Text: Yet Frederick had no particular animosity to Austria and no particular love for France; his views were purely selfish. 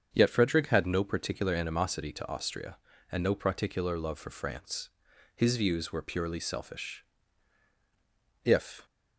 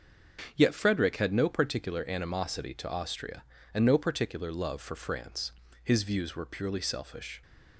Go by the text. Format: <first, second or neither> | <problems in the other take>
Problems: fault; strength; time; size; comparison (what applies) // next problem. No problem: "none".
second | starts louder than the rest; strong; until 1.1 s; 7.5 dB; also in the second // goes on to say "If"; slight; from 8.4 s on; 0.42 s long